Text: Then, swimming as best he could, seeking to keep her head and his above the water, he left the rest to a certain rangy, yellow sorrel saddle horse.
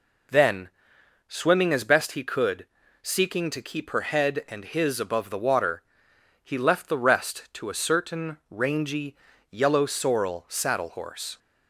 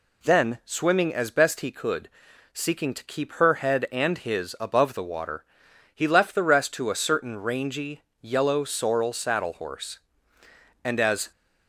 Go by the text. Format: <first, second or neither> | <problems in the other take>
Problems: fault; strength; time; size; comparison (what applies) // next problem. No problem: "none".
first | goes on to say "And as"; slight; from 10.8 s on; 0.48 s long